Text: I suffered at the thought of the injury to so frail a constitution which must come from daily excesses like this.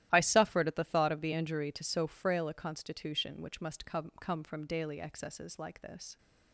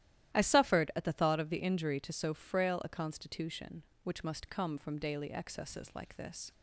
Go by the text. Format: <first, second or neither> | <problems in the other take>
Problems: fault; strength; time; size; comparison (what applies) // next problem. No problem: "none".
second | starts louder than the rest; strong; until 1.1 s; 13 dB; strong in the second // says "come" twice; at 4.2 s